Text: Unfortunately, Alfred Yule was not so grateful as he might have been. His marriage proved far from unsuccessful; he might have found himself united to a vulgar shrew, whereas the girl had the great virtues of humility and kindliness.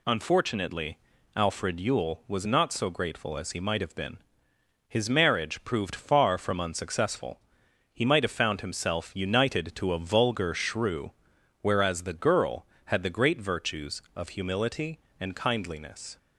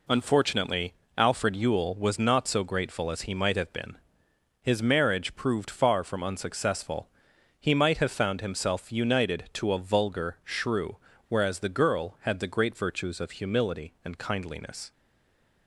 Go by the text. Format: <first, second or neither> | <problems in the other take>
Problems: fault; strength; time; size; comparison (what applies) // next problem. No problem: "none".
first | stays silent after the last word; slight; from 14.9 s on; 0.7 s long